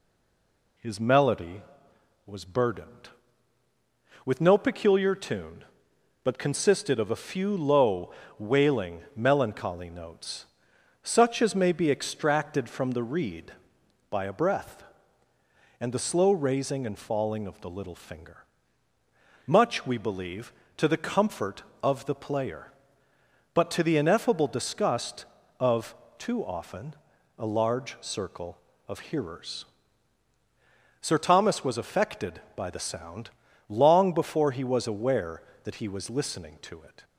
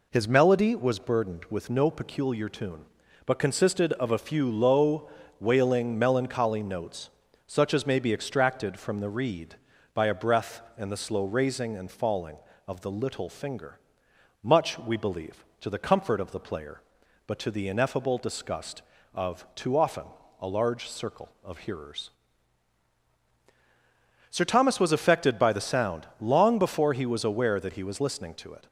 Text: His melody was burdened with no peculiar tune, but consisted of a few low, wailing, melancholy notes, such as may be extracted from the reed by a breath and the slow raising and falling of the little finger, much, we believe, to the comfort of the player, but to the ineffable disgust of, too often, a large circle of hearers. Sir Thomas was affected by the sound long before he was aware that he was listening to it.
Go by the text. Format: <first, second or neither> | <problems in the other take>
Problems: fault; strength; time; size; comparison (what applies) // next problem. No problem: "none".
second | stays silent before the first word; slight; until 0.7 s; 0.7 s long // pauses between "sound" and "long"; at 33.2 s; 0.40 s long